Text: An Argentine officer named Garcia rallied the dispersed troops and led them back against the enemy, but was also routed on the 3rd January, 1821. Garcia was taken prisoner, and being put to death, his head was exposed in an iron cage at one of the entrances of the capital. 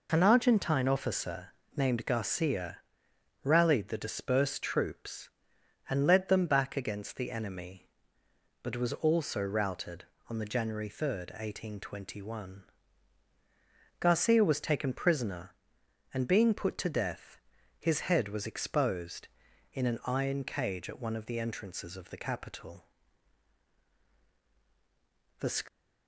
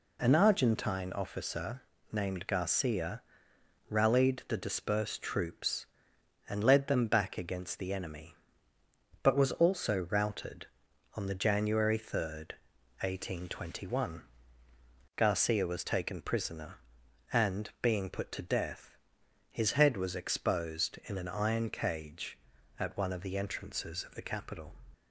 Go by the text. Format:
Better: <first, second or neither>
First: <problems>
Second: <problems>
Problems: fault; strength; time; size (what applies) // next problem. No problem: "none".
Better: second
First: pauses between "officer" and "named"; slight; at 1.5 s; 0.26 s long // pauses between "Garcia" and "rallied"; noticeable; at 2.8 s; 0.64 s long // goes on to say "The"; slight; from 25.3 s on; 0.24 s long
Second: pauses between "officer" and "named"; slight; at 1.8 s; 0.32 s long // pauses between "Garcia" and "rallied"; noticeable; at 3.2 s; 0.66 s long